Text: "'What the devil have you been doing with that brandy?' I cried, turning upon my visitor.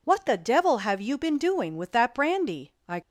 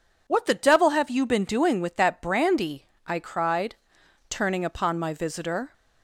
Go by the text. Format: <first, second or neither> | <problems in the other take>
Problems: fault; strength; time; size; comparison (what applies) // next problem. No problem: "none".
second | stops before "cried turning upon my visitor"; at 3.0 s